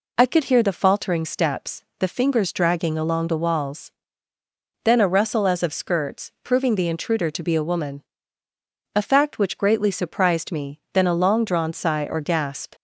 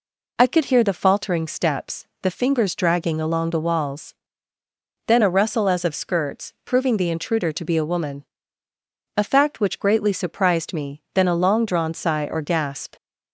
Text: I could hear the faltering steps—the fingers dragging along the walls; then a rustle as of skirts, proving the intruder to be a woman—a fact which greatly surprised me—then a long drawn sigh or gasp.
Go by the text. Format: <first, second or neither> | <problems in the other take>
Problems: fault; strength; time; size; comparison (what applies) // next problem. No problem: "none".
neither | none